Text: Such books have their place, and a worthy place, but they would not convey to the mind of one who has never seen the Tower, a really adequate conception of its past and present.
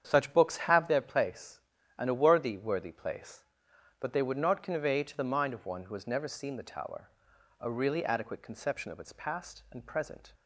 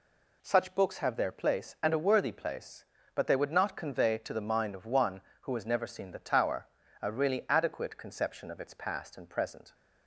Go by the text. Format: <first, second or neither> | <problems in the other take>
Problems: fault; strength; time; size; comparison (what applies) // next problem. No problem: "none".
second | starts louder than the rest; strong; until 1.0 s; 8.5 dB // says "worthy" twice; at 2.5 s